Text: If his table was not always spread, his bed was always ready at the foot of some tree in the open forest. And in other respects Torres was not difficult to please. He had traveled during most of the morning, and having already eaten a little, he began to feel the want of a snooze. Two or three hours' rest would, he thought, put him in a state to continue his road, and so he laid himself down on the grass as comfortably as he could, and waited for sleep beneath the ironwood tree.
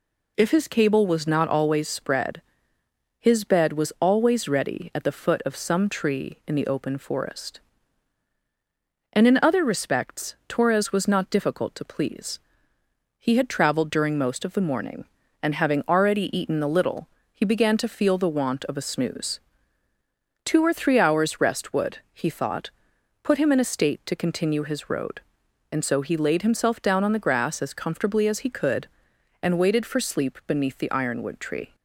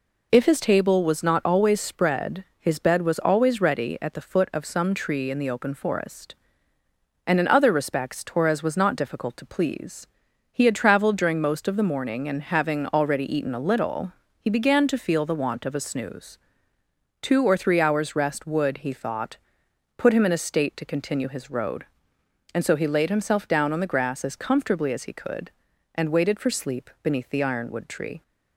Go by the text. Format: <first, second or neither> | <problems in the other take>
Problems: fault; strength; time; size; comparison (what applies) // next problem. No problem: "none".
second | says "cable" for "table"; at 0.6 s